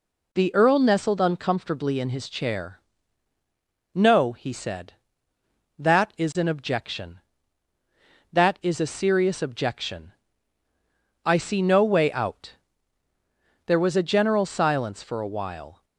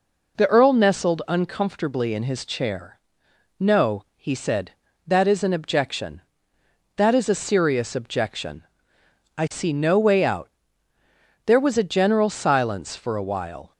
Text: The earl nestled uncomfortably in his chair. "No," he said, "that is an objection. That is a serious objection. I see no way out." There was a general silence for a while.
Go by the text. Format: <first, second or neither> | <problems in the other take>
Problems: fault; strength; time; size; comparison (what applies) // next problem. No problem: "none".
neither | none